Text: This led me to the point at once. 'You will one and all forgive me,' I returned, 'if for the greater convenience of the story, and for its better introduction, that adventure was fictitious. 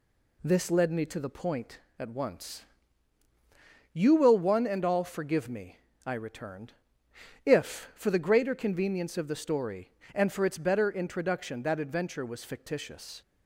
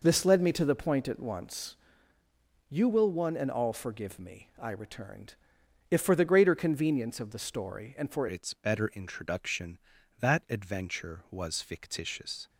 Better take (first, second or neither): first